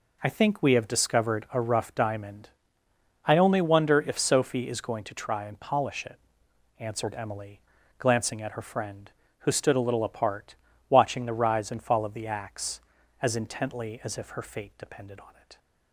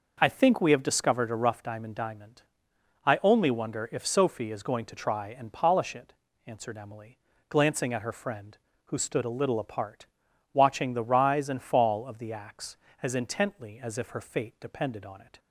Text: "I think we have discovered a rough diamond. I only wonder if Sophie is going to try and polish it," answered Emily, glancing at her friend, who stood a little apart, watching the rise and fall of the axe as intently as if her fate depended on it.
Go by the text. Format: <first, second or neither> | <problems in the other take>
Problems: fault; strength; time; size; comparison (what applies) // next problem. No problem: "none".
first | says "diamond" twice; at 1.9 s